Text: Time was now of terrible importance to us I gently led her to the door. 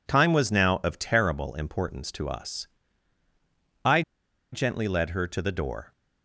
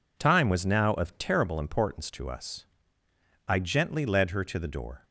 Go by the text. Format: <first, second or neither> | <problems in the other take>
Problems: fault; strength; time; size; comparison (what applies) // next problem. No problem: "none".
second | pauses between "us" and "I"; at 2.6 s; 1.1 s long; noticeable in the second // pauses between "I" and "gently"; noticeable; at 4.0 s; 0.51 s long